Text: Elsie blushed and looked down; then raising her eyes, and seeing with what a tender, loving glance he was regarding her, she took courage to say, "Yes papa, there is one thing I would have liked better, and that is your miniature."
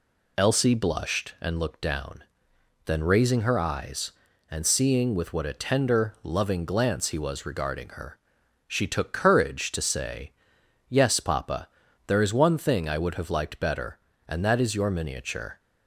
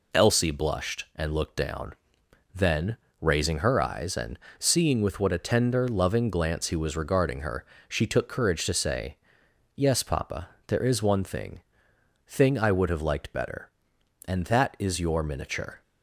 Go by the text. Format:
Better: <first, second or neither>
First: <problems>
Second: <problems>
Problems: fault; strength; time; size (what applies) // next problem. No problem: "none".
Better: first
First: none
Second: pauses between "then" and "raising"; slight; at 2.9 s; 0.24 s long // pauses between "and" and "seeing"; slight; at 4.3 s; 0.20 s long // says "thing" twice; at 12.2 s